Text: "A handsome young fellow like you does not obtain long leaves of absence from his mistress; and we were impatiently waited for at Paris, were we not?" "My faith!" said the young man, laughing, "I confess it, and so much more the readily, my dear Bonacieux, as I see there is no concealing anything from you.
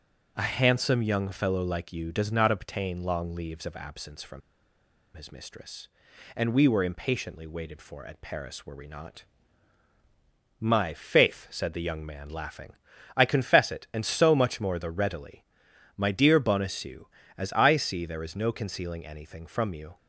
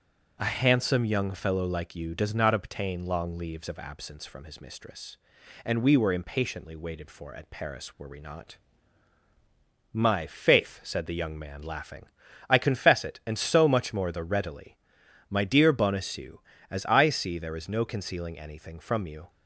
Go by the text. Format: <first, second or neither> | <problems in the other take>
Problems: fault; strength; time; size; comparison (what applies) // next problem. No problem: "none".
second | starts louder than the rest; noticeable; until 1.3 s; 6 dB; noticeable in the second // pauses between "from" and "his"; noticeable; at 4.4 s; 0.76 s long